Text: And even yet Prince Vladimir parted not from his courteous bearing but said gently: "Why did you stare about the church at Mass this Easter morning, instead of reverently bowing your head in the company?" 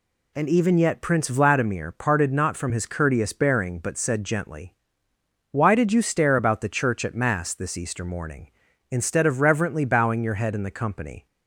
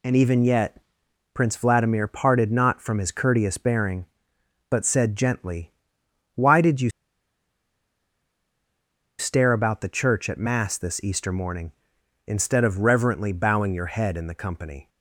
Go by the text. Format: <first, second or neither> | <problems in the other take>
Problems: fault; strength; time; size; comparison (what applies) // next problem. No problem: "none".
first | pauses between "yet" and "Prince"; noticeable; at 0.7 s; 0.56 s long // pauses between "you" and "stare"; strong; at 6.8 s; 2.3 s long